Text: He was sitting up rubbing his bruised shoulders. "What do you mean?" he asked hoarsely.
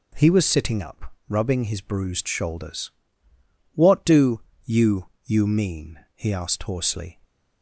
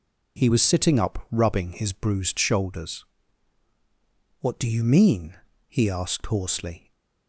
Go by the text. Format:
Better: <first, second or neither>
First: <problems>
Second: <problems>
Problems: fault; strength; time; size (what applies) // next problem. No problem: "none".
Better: second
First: pauses between "up" and "rubbing"; slight; at 1.1 s; 0.18 s long // pauses between "do" and "you"; slight; at 4.3 s; 0.24 s long // says "you" twice; at 5.2 s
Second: none